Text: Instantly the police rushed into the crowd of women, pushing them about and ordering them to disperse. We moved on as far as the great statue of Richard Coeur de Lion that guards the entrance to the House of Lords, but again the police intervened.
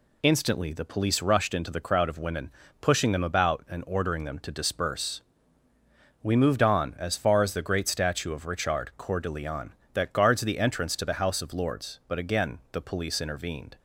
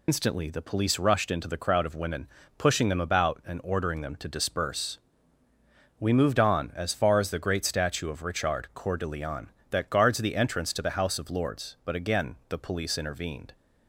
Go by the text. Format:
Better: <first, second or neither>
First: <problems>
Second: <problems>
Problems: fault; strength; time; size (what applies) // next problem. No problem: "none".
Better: first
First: none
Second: loses the start of "Instantly"; at 0.0 s; 90 ms